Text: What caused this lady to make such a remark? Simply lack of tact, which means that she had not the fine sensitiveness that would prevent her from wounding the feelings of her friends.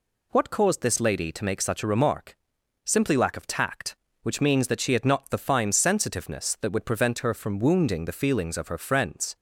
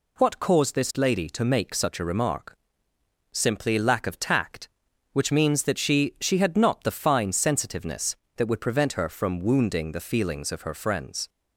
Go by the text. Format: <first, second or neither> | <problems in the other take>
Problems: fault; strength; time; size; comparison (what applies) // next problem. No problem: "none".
first | says "she" twice; at 6.1 s